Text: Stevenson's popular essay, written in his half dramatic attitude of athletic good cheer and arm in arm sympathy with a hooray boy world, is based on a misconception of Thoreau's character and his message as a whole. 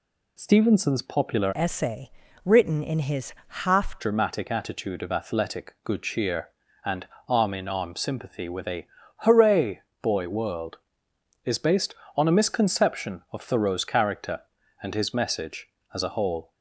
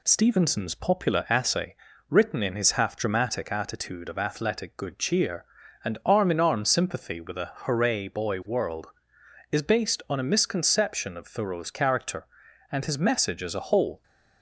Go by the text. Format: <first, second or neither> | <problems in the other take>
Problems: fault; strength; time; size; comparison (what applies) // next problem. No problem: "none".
second | changes voice from "essay" to "half"; from 1.5 to 3.9 s; 2.4 s long // pauses between "and" and "arm"; slight; at 7.0 s; 0.24 s long // pauses between "a" and "hooray"; slight; at 8.8 s; 0.30 s long // pauses between "hooray" and "boy"; slight; at 9.8 s; 0.20 s long